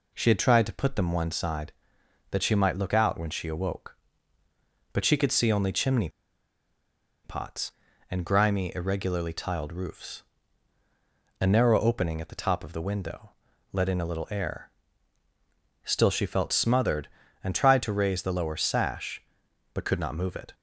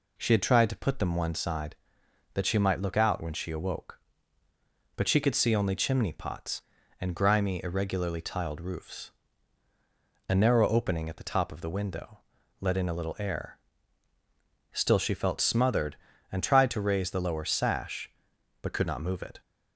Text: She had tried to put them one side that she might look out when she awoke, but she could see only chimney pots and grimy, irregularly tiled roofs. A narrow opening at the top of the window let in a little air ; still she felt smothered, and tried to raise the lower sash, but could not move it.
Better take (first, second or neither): second